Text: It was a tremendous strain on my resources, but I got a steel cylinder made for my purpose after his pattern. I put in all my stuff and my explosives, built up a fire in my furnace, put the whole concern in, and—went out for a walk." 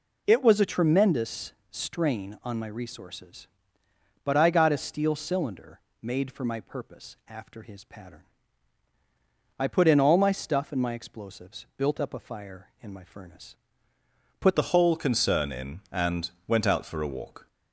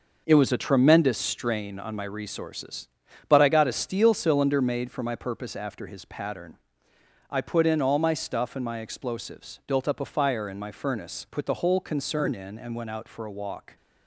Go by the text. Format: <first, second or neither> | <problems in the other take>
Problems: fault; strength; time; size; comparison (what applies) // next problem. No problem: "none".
second | pauses between "tremendous" and "strain"; slight; at 1.5 s; 0.16 s long // pauses between "cylinder" and "made"; slight; at 5.8 s; 0.20 s long // changes voice at "the"; from 14.5 s on; 2.9 s long